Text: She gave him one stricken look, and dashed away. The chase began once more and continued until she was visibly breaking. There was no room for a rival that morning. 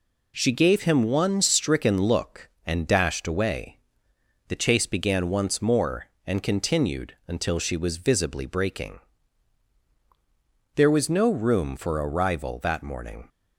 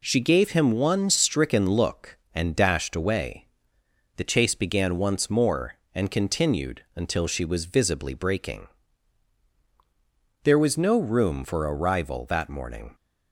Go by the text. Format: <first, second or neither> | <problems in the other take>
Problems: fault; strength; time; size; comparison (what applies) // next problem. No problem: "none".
neither | none